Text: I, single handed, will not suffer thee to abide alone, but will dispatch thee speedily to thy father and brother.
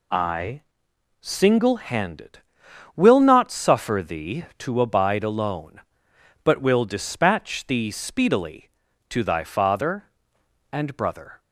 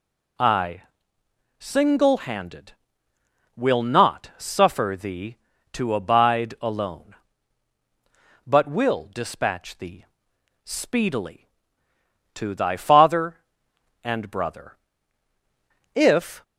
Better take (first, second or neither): first